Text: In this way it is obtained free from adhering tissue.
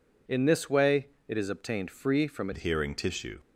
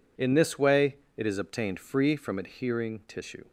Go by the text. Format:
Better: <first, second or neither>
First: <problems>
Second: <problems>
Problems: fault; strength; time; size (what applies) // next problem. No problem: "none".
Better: second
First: pauses between "way" and "it"; slight; at 1.0 s; 0.20 s long // changes voice at "adhering"; from 2.5 s on; 0.8 s long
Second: pauses between "way" and "it"; slight; at 0.9 s; 0.20 s long